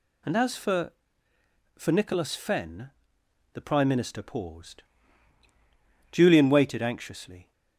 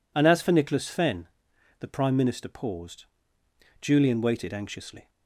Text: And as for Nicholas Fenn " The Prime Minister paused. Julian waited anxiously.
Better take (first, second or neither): second